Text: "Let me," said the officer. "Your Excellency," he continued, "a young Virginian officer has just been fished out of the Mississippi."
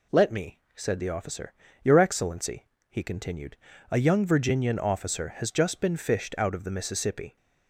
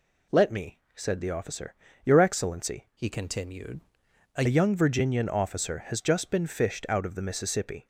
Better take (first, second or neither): first